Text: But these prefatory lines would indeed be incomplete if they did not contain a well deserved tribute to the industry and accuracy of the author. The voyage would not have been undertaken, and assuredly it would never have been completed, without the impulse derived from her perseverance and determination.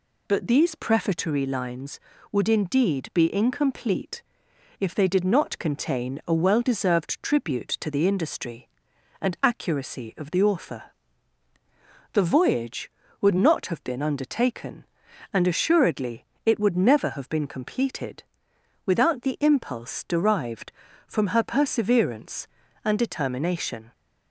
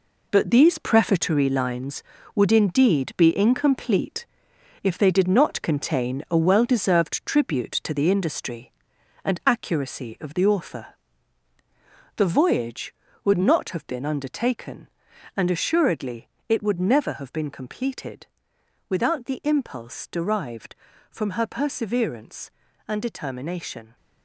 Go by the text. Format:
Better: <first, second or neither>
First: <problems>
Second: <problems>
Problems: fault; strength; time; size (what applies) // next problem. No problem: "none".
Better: first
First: pauses between "incomplete" and "if"; noticeable; at 4.2 s; 0.58 s long // pauses between "assuredly" and "it"; slight; at 16.2 s; 0.20 s long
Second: gets quieter; strong; throughout; 9 dB // pauses between "incomplete" and "if"; noticeable; at 4.2 s; 0.58 s long // pauses between "assuredly" and "it"; slight; at 16.2 s; 0.20 s long